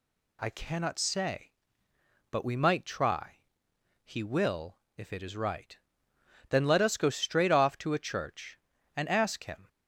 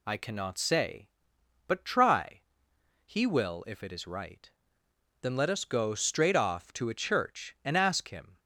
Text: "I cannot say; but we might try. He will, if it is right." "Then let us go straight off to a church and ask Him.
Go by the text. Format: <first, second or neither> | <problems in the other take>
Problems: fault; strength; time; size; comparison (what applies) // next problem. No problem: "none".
first | skips "we might"; at 1.8 s